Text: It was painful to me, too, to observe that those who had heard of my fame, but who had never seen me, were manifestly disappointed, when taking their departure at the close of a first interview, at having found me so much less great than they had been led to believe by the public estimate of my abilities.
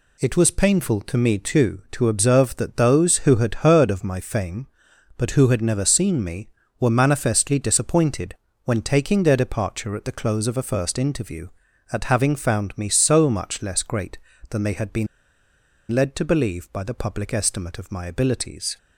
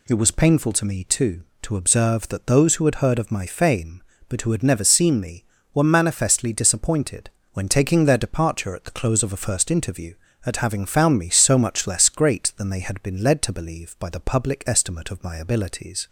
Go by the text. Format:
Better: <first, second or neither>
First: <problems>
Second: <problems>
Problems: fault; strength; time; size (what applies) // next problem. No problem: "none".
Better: second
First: pauses between "been" and "led"; noticeable; at 15.0 s; 0.84 s long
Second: none